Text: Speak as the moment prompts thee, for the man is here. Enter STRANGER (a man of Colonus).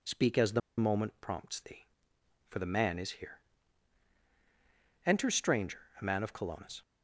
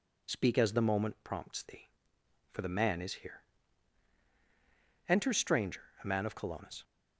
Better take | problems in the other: second | pauses between "the" and "moment"; slight; at 0.6 s; 0.19 s long

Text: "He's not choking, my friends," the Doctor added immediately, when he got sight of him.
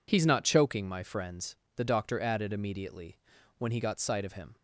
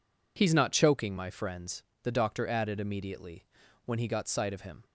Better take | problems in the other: neither | none

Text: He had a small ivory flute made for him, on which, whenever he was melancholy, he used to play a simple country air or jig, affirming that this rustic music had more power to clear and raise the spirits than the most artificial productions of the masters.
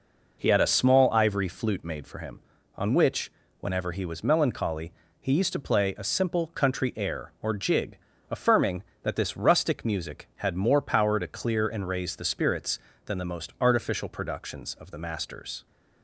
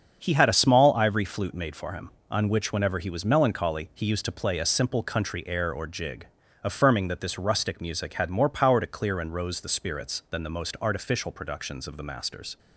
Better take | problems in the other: first | starts louder than the rest; strong; until 1.2 s; 7 dB // says "rose" for "raise"; at 9.3 s

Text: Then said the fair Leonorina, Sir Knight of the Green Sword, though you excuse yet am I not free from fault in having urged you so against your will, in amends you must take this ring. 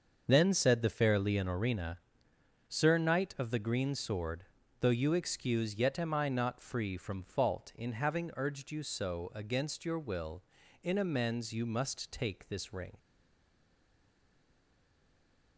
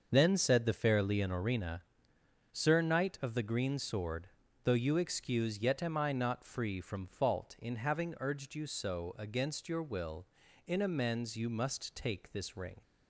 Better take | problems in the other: second | starts louder than the rest; until 1.2 s; 6.5 dB; also in the second // stays silent after the last word; strong; from 12.9 s on; 2.6 s long

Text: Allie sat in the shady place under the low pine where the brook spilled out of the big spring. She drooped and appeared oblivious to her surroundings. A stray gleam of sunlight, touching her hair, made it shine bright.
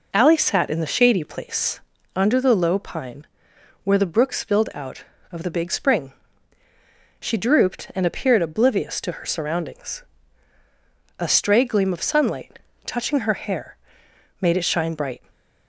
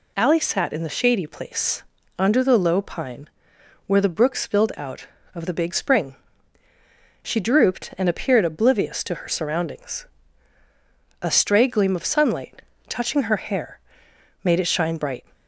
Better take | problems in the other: second | starts louder than the rest; noticeable; until 1.6 s; 4.5 dB // pauses between "place" and "under"; slight; at 1.8 s; 0.36 s long; slight in the second // pauses between "pine" and "where"; noticeable; at 3.2 s; 0.58 s long; noticeable in the second

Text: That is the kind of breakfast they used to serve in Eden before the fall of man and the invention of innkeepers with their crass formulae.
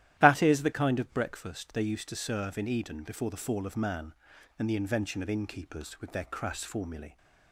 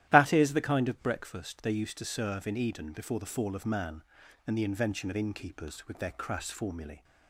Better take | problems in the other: neither | starts louder than the rest; strong; the same in both

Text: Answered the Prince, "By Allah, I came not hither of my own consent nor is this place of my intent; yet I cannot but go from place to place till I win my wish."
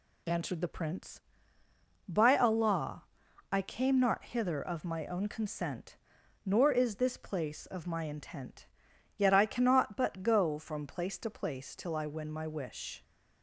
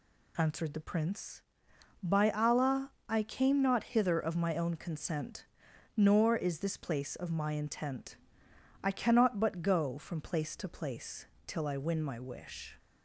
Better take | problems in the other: first | pauses between "consent" and "nor"; noticeable; at 5.4 s; 0.50 s long; noticeable in the first // skips "yet"; at 8.5 s // pauses between "place" and "till"; slight; at 11.2 s; 0.22 s long

